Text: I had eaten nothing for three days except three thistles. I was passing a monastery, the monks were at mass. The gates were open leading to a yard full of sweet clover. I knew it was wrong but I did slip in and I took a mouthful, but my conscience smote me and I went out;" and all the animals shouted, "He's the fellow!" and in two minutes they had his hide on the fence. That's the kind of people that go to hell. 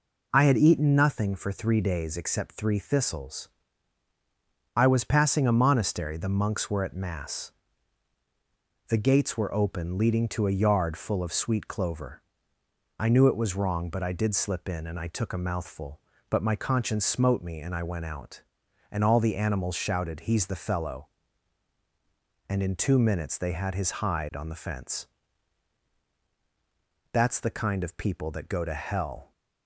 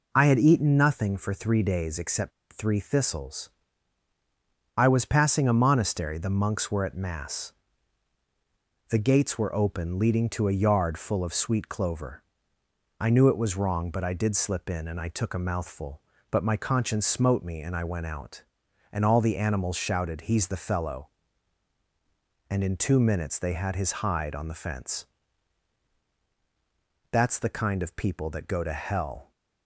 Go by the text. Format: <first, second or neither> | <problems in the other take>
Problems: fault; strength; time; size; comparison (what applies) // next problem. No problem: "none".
first | pauses between "except" and "three"; slight; at 2.3 s; 0.22 s long